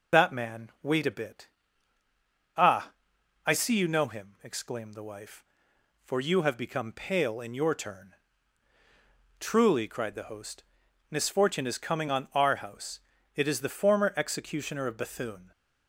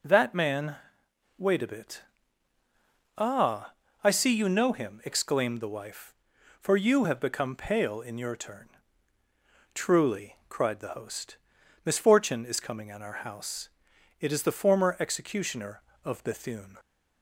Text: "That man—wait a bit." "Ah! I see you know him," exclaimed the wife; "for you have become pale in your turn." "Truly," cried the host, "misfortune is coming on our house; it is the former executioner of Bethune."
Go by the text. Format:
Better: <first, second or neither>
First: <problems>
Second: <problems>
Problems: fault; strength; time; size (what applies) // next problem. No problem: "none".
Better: second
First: loses the start of "That"; at 0.1 s; 105 ms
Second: none